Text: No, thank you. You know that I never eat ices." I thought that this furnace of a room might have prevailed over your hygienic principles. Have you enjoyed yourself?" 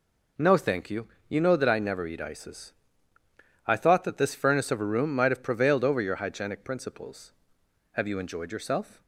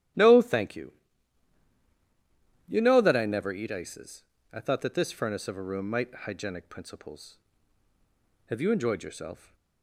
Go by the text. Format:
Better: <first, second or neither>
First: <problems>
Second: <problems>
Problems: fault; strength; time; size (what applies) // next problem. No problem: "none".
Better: first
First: none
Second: starts louder than the rest; strong; until 2.9 s; 12 dB // skips "have prevailed over your"; at 6.1 s